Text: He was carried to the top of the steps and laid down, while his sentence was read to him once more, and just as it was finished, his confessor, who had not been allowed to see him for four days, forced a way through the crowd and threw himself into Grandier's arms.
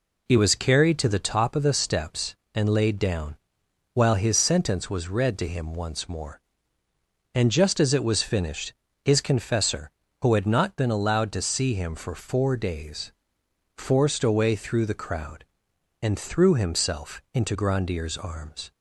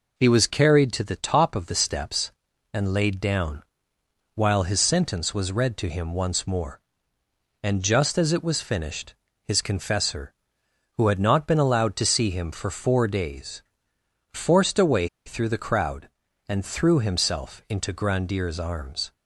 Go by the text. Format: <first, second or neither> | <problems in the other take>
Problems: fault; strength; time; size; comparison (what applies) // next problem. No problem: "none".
first | pauses between "way" and "through"; slight; at 15.0 s; 0.19 s long